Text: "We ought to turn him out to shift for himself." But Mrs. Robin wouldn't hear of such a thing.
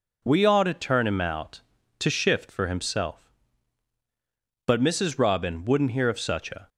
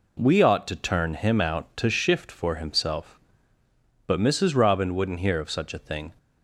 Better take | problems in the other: second | stops before "thing"; at 6.6 s

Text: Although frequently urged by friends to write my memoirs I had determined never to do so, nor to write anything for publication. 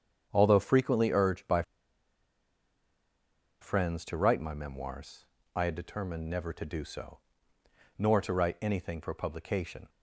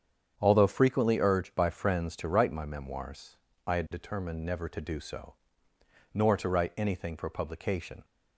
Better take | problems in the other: second | starts louder than the rest; strong; until 1.3 s; 8 dB; strong in the second // pauses between "by" and "friends"; strong; at 1.6 s; 1.9 s long // pauses between "memoirs" and "I"; slight; at 5.2 s; 0.28 s long; slight in the second

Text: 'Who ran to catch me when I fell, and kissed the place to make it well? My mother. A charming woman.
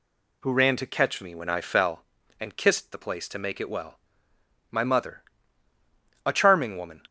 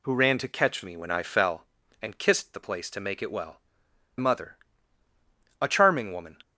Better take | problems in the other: first | skips "My"; at 3.8 s

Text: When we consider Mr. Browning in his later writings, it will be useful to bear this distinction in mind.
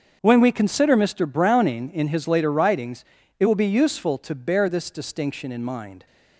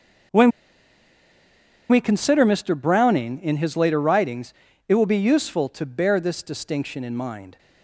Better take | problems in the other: first | starts louder than the rest; until 2.7 s; 7 dB; also in the first // pauses between "When" and "we"; strong; at 0.5 s; 1.3 s long

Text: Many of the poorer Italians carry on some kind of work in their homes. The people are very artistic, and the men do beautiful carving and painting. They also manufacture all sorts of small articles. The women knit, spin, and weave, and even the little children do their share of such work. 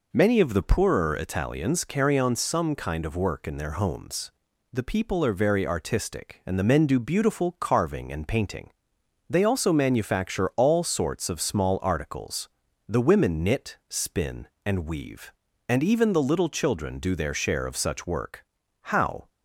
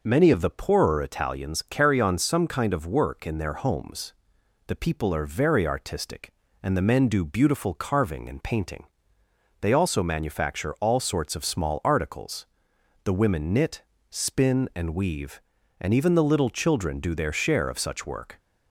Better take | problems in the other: second | goes on to say "How"; slight; from 18.8 s on; 0.48 s long

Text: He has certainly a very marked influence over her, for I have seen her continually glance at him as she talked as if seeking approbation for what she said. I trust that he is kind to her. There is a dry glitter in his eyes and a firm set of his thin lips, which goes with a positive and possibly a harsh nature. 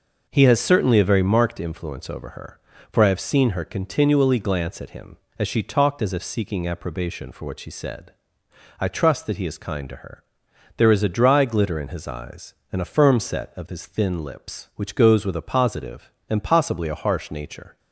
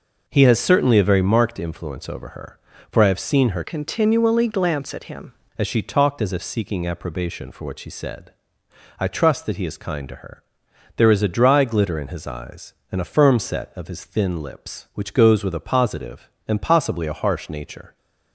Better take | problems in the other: first | changes voice from "continually" to "him"; from 3.6 to 5.3 s; 1.7 s long

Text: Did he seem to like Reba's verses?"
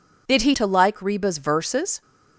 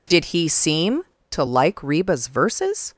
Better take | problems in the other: second | skips "seem"; at 0.5 s

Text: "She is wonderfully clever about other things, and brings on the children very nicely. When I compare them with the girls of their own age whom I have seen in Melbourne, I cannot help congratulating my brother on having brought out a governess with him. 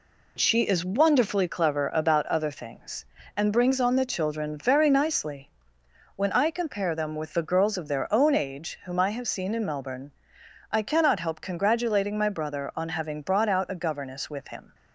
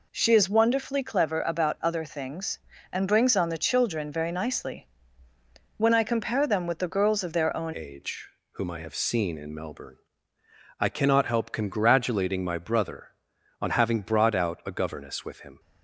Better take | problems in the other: first | changes voice at "age"; from 7.7 s on; 7.8 s long // pauses between "age" and "whom"; slight; at 8.2 s; 0.24 s long

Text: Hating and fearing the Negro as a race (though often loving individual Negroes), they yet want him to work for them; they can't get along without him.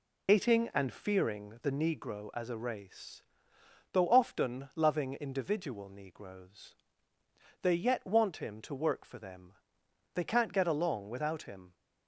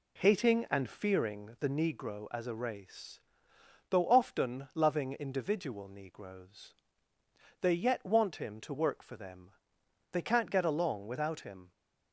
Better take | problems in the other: second | loses the start of "Hating"; at 0.2 s; 100 ms

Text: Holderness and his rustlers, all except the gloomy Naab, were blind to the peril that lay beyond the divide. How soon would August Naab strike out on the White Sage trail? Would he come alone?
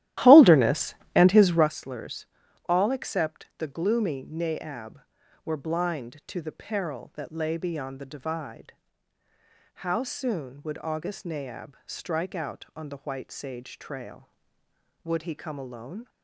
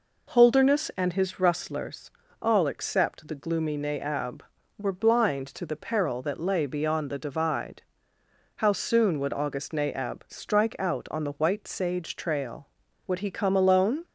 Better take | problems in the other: second | starts louder than the rest; strong; until 1.7 s; 14 dB

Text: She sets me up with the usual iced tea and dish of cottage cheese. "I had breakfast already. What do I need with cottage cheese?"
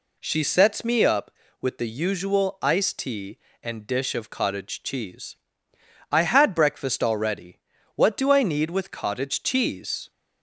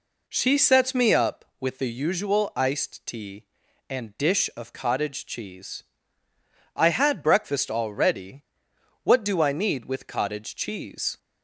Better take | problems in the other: neither | none

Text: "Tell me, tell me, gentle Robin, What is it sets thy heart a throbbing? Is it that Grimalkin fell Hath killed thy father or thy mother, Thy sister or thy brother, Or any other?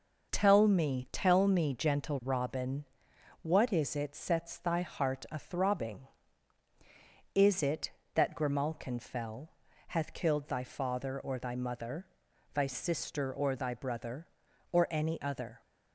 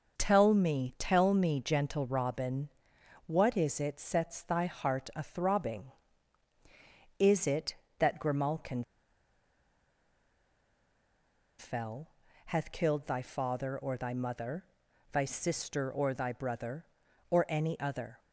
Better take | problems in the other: first | pauses between "Grimalkin" and "fell"; strong; at 8.8 s; 2.7 s long // pauses between "fell" and "Hath"; at 12.0 s; 0.38 s long; also in the first

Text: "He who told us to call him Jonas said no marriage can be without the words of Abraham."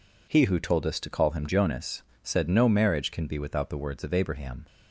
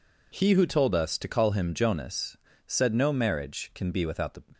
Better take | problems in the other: first | pauses between "Jonas" and "said"; slight; at 2.3 s; 0.28 s long; slight in the first // stops before "words of Abraham"; at 4.5 s

